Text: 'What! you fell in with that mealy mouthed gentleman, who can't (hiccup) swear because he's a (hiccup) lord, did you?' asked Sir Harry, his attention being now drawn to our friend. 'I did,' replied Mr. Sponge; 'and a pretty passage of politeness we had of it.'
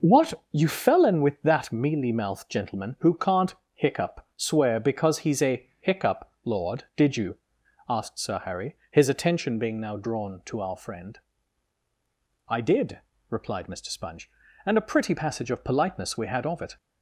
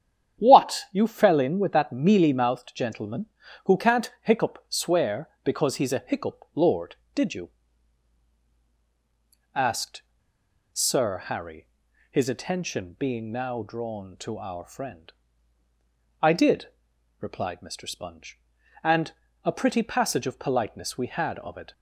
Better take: first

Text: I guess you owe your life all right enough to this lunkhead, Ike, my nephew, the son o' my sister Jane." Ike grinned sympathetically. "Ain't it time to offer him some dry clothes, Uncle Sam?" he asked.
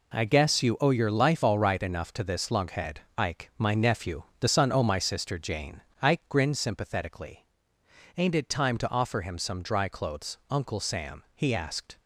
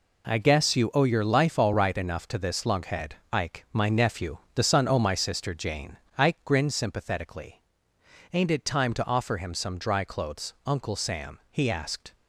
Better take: neither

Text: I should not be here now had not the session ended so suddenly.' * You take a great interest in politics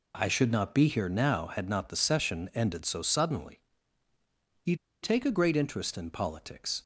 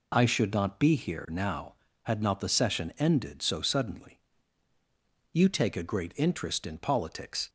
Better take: second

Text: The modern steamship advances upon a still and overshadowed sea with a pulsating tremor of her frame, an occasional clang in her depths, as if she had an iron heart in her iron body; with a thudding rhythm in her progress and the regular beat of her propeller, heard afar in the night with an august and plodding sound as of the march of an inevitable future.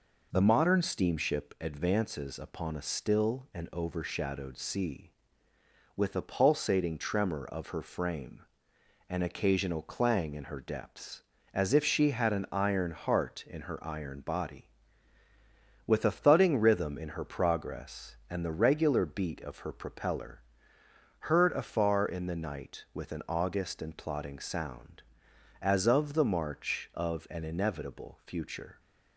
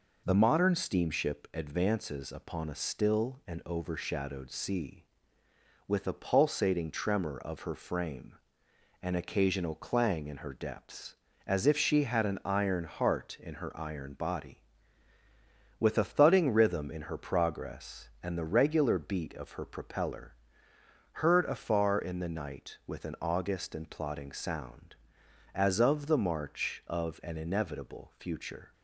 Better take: neither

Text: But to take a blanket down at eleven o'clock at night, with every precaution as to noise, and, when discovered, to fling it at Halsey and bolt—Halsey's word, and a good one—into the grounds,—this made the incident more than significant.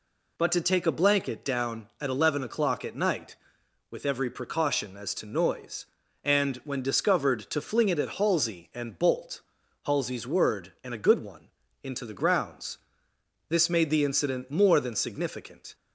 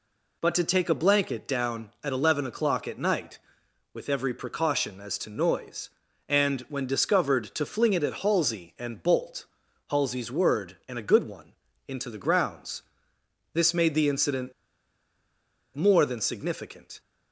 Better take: first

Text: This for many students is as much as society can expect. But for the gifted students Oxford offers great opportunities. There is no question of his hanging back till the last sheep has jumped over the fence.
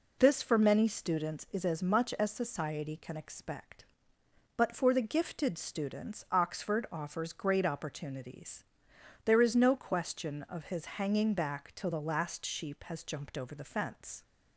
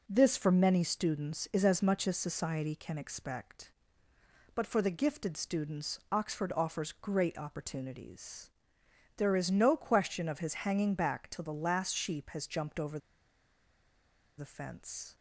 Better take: first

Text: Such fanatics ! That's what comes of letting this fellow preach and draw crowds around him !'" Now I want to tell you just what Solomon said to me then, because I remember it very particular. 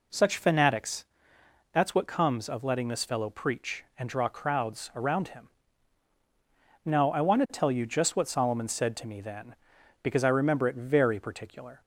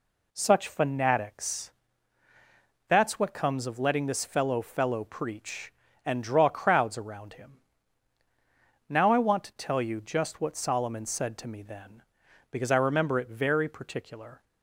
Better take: first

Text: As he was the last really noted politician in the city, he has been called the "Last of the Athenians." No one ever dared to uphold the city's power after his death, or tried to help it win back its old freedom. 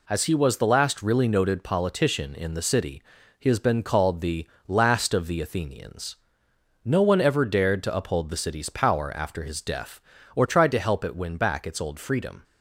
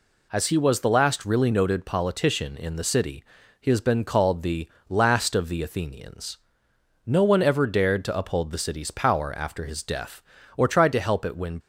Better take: first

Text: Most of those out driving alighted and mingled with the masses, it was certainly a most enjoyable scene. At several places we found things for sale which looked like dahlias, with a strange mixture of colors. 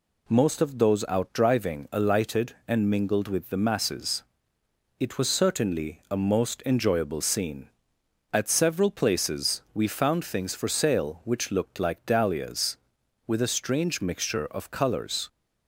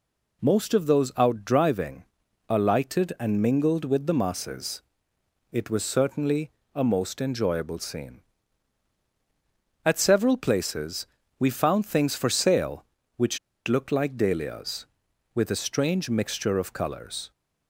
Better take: first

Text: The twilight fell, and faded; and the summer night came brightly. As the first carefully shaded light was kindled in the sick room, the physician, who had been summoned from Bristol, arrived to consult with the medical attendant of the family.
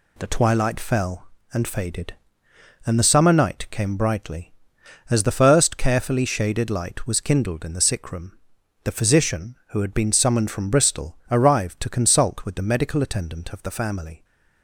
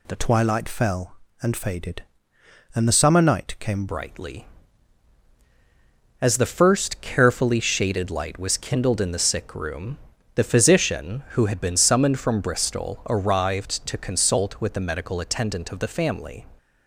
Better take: first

